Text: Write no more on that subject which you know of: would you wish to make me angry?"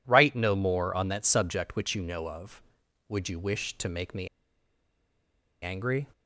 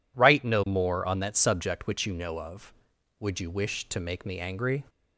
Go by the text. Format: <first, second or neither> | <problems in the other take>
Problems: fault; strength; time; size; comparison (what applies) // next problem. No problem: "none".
second | pauses between "me" and "angry"; strong; at 4.2 s; 1.3 s long